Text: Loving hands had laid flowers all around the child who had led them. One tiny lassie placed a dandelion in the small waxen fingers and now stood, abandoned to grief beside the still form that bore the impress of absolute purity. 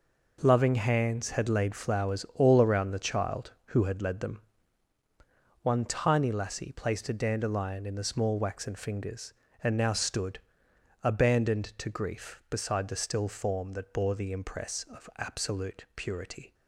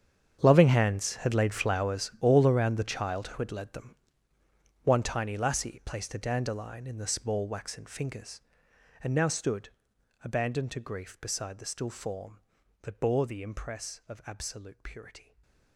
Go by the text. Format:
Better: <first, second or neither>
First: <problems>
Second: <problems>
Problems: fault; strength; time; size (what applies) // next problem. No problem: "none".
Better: first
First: none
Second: gets quieter; strong; throughout; 17 dB // stays silent after the last word; slight; from 15.1 s on; 0.6 s long